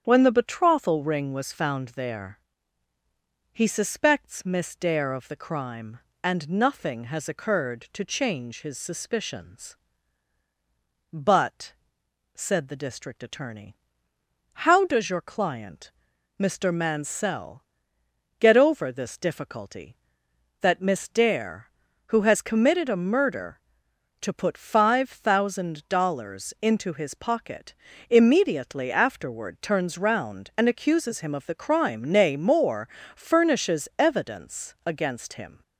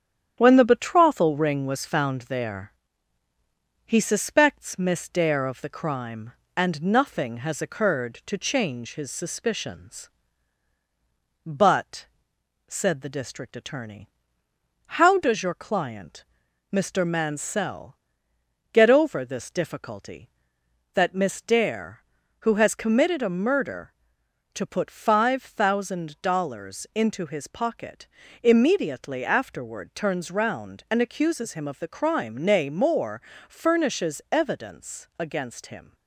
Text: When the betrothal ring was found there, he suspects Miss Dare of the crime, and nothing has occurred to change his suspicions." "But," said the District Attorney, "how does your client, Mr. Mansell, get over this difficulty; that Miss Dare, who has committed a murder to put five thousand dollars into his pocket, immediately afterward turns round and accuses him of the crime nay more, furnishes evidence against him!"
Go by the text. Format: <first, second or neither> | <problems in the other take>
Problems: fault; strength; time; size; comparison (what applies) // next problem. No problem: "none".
first | gets quieter; slight; throughout; 2.5 dB // starts louder than the rest; strong; until 1.3 s; 9.5 dB; strong in the first